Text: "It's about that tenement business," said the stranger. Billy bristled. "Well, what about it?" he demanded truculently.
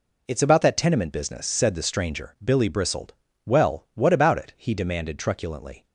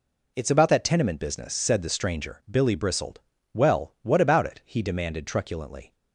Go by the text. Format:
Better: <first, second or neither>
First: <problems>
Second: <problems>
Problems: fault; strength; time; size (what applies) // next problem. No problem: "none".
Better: neither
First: none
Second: none